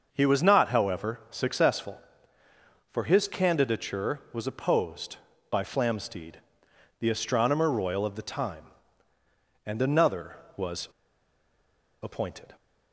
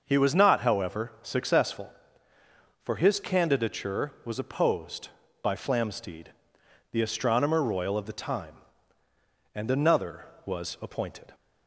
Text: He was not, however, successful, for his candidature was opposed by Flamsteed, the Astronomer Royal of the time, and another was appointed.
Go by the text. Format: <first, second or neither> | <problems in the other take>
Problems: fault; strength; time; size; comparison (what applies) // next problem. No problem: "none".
second | starts louder than the rest; until 1.1 s; 6 dB; also in the second // pauses between "was" and "appointed"; at 10.8 s; 1.1 s long